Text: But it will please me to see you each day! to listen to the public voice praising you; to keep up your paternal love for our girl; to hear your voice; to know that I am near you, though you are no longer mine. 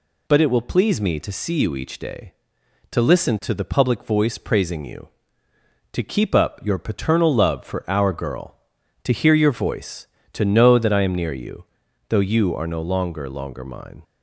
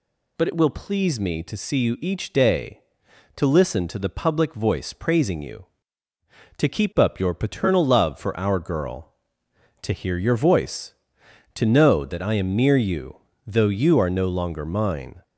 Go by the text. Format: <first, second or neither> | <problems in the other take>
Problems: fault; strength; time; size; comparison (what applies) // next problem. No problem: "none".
second | says "longer" twice; at 13.2 s